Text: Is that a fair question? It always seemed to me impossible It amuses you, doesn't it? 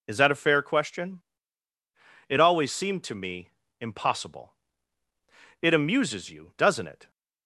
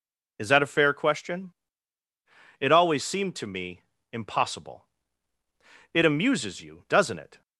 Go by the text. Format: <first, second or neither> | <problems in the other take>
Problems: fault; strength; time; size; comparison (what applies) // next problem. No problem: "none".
neither | pauses between "me" and "impossible"; slight; the same in both // pauses between "impossible" and "It"; the same in both